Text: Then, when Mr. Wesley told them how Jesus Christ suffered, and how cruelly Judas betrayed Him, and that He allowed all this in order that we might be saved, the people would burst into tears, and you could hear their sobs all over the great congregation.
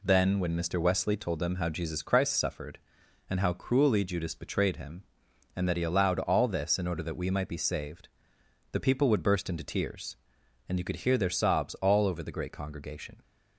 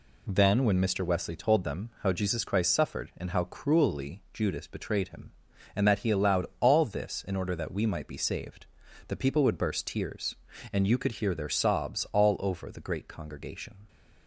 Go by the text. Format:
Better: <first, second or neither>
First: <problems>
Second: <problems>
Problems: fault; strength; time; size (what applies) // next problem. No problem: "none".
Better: first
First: none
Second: skips "into"; at 9.8 s